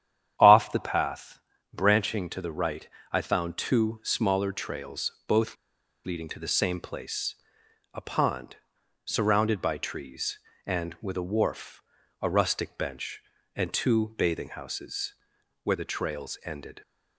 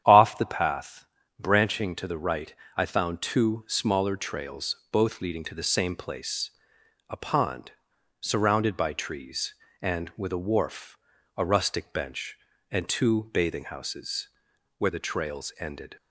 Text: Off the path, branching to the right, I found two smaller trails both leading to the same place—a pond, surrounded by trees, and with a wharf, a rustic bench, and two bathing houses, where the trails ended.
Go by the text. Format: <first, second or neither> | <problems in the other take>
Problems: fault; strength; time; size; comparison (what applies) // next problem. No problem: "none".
second | starts louder than the rest; strong; until 1.3 s; 9.5 dB; strong in the second // pauses between "both" and "leading"; noticeable; at 5.5 s; 0.50 s long